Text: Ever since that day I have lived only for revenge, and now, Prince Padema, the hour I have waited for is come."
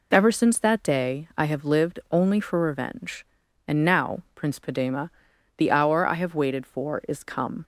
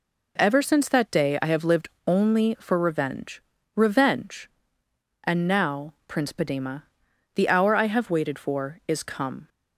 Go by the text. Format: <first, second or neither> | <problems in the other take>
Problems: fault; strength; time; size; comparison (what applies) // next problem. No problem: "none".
first | pauses between "lived" and "only"; slight; at 1.8 s; 0.18 s long // says "revenge" twice; at 3.7 s